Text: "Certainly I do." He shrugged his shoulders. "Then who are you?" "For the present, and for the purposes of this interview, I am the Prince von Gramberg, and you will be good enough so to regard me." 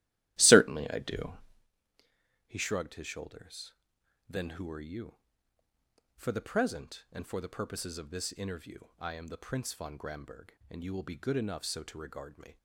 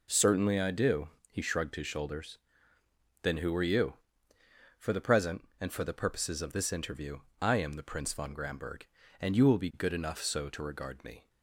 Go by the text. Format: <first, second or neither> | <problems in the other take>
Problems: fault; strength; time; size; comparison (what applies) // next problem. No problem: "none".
second | starts louder than the rest; strong; until 1.7 s; 14.5 dB